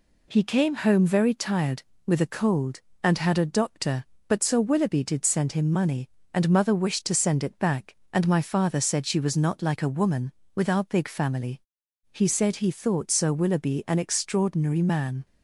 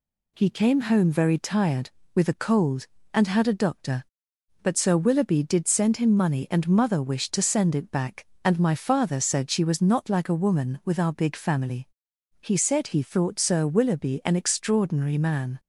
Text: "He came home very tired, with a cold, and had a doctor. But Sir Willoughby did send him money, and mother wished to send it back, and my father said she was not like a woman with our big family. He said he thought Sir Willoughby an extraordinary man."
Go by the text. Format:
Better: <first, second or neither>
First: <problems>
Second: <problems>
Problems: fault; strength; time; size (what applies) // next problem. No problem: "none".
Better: neither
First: none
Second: none